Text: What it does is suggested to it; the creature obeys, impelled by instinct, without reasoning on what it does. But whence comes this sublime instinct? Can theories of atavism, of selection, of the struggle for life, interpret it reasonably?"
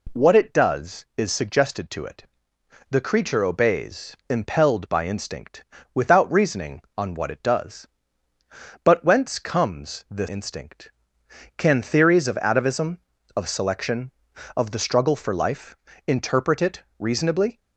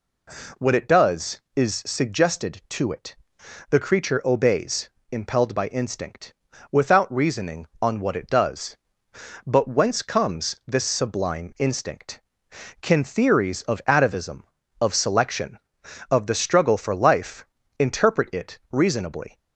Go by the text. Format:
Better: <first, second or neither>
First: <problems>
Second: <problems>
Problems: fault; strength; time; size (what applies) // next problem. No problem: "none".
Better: second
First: skips "sublime"; at 10.2 s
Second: none